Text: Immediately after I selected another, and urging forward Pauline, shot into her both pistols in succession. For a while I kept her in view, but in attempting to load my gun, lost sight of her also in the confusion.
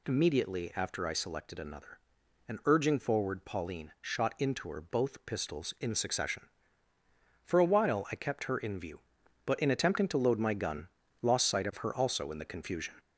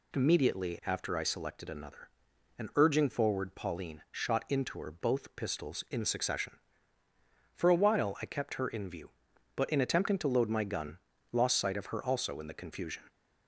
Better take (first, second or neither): second